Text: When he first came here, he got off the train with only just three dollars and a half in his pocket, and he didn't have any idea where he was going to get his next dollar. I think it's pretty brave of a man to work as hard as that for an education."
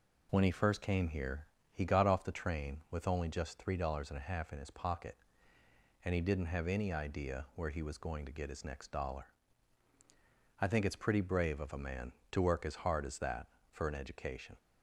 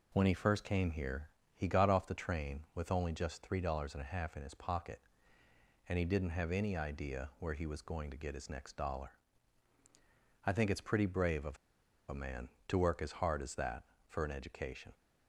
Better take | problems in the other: first | pauses between "of" and "a"; noticeable; at 11.5 s; 0.51 s long

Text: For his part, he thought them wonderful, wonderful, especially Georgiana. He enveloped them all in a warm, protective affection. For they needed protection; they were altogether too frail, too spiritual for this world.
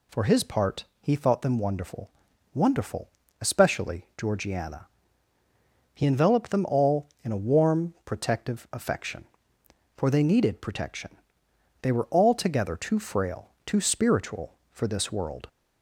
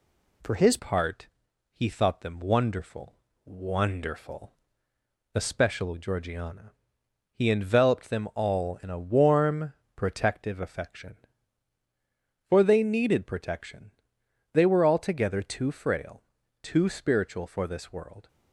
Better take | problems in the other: first | changes voice at "part"; from 0.7 s on; 17.5 s long

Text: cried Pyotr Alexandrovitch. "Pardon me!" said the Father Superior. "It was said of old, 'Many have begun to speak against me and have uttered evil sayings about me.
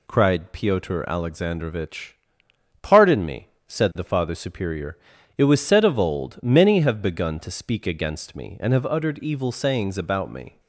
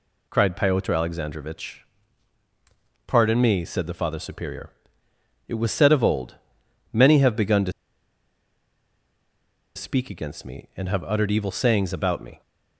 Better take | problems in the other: first | pauses between "to" and "speak"; strong; at 7.7 s; 2.0 s long

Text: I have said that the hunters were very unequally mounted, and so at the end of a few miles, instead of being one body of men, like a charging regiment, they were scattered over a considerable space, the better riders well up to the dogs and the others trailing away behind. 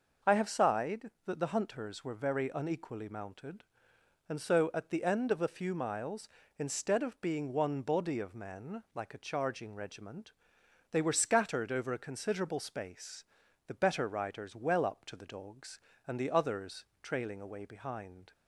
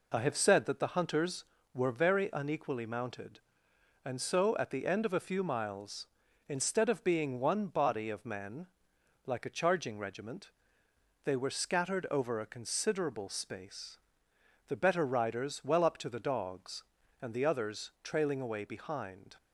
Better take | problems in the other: second | says "sighed" for "said"; at 0.4 s // pauses between "others" and "trailing"; slight; at 16.8 s; 0.16 s long

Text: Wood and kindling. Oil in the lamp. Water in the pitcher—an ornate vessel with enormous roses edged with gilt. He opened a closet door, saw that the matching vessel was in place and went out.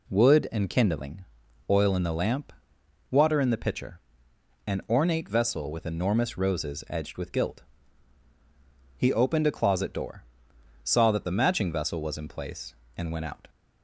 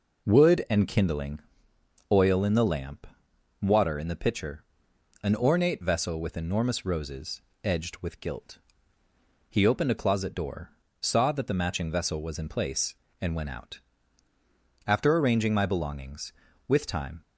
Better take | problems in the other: first | pauses between "roses" and "edged"; slight; at 7.4 s; 0.22 s long // goes on to say "After arranging my belongings with time"; strong; from 14.8 s on; 2.3 s long

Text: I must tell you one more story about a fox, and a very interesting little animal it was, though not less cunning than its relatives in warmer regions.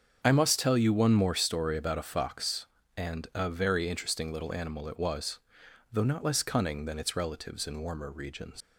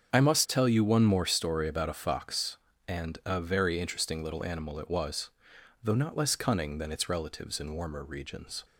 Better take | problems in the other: second | starts louder than the rest; strong; until 1.2 s; 7 dB; strong in the second // leaves "regions" unfinished; at 8.6 s; 115 ms

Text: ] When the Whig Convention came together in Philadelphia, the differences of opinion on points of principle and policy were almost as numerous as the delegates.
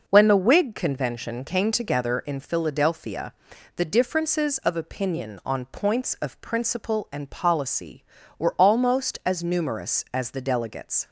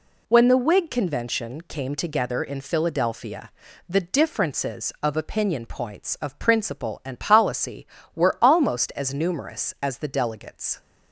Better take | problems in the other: first | skips "on"; at 5.6 s

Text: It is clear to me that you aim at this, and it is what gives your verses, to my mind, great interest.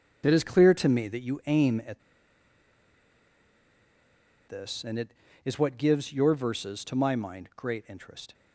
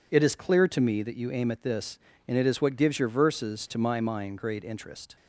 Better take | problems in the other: second | starts louder than the rest; until 1.2 s; 6.5 dB // pauses between "at" and "this"; strong; at 2.0 s; 2.4 s long

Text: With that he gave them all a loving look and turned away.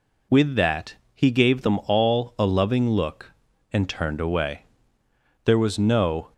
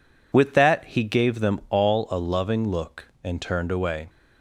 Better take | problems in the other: second | pauses between "that" and "he"; slight; at 0.9 s; 0.20 s long // goes on to say "There was no"; noticeable; from 5.4 s on; 0.88 s long

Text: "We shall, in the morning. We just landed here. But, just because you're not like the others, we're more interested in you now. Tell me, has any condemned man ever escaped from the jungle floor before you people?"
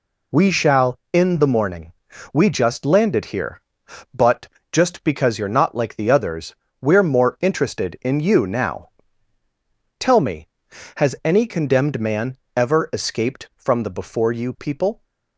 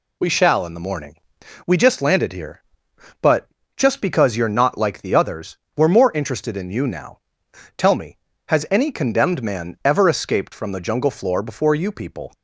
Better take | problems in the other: second | pauses between "man" and "ever"; slight; at 12.3 s; 0.18 s long // skips "jungle floor"; at 13.9 s

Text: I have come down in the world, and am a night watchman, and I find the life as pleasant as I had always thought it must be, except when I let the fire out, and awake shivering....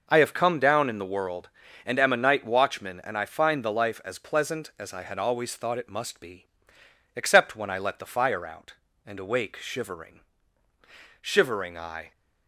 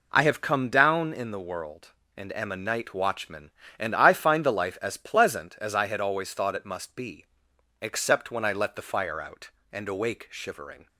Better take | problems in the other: second | goes on to say "Shivering I"; noticeable; from 11.2 s on; 0.90 s long

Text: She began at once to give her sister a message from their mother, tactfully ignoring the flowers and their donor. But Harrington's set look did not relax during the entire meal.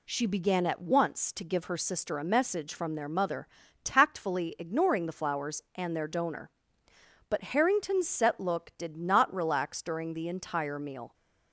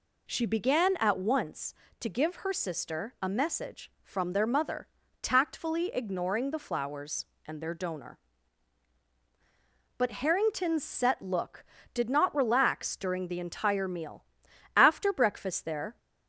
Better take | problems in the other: first | goes on to say "After breakfast there"; noticeable; from 14.7 s on; 1.2 s long

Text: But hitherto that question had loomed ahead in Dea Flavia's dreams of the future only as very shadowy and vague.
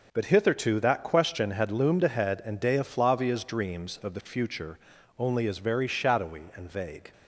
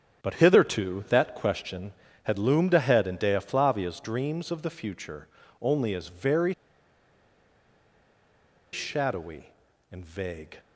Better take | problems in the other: first | starts louder than the rest; strong; until 1.2 s; 7.5 dB // pauses between "future" and "only"; slight; at 5.2 s; 0.34 s long; also in the first // pauses between "very" and "shadowy"; strong; at 6.5 s; 2.1 s long

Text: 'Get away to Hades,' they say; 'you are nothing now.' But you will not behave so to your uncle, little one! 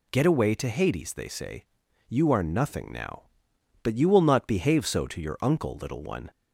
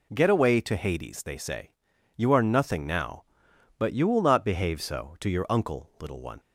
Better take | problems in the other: neither | none

